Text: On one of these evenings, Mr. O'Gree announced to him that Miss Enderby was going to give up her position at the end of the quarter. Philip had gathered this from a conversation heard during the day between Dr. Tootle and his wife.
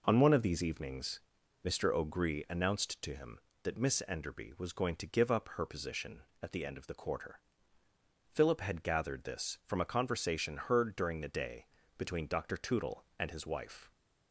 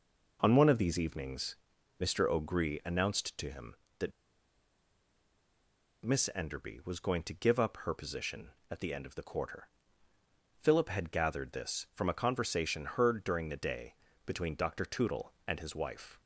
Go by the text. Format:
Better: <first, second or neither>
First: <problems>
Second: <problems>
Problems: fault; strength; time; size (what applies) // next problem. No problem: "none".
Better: first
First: pauses between "day" and "between"; slight; at 11.6 s; 0.28 s long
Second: pauses between "that" and "Miss"; strong; at 4.1 s; 1.9 s long // pauses between "day" and "between"; slight; at 13.9 s; 0.28 s long